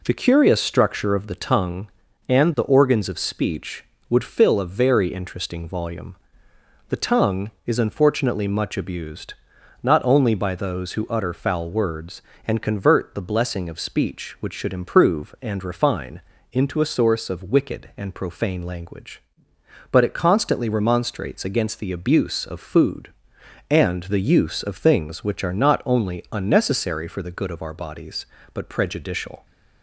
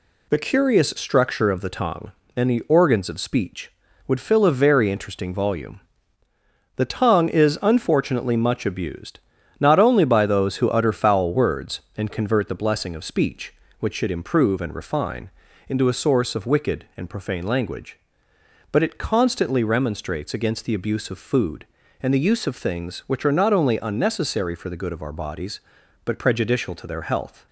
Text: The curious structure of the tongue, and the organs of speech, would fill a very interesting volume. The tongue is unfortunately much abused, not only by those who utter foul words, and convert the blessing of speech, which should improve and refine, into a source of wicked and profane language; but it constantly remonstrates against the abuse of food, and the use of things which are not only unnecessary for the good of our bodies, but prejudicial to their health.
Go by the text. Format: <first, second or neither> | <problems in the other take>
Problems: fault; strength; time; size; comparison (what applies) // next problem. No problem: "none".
second | stops before "to their health"; at 29.4 s